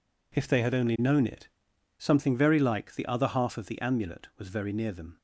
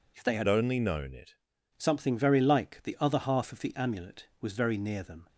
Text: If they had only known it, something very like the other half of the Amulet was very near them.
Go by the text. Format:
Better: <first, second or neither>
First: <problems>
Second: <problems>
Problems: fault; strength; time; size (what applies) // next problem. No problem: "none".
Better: first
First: none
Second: changes voice from "only" to "it"; from 0.4 to 1.3 s; 0.9 s long